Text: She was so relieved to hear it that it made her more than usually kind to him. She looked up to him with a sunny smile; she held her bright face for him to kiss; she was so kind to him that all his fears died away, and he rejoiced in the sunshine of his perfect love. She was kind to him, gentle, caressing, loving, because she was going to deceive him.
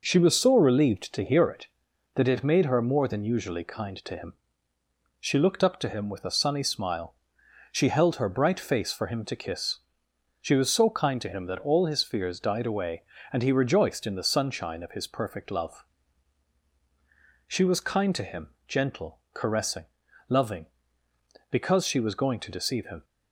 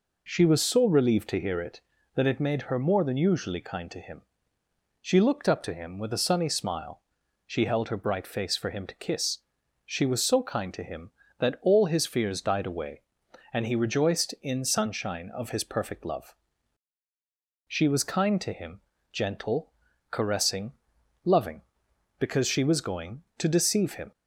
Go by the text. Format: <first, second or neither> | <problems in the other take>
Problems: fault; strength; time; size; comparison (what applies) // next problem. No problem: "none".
first | skips "the"; at 14.6 s